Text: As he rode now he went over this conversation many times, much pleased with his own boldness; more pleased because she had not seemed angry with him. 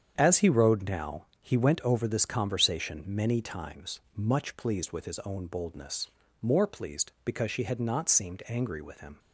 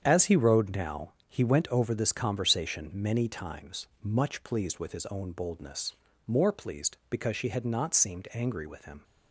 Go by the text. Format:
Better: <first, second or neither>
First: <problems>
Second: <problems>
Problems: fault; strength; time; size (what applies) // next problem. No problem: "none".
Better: neither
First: starts louder than the rest; strong; until 1.1 s; 8 dB // pauses between "now" and "he"; slight; at 1.2 s; 0.16 s long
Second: starts louder than the rest; strong; until 1.0 s; 8 dB // pauses between "now" and "he"; slight; at 1.1 s; 0.16 s long